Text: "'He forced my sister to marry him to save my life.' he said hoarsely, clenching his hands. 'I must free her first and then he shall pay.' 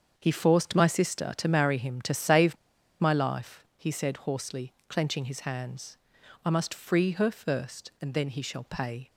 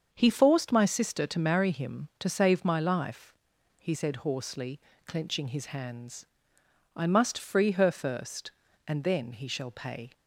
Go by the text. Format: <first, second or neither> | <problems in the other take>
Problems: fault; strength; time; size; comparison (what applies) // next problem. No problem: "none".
second | starts louder than the rest; until 1.1 s; 7 dB; also in the second // pauses between "save" and "my"; at 2.5 s; 0.45 s long